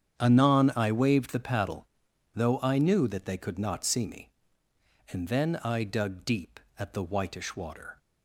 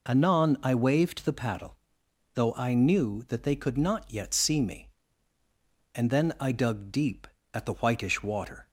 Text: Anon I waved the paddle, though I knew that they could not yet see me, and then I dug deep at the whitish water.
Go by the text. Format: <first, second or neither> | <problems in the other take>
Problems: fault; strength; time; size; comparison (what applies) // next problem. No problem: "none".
second | starts louder than the rest; strong; until 1.2 s; 8.5 dB // skips "yet"; at 3.8 s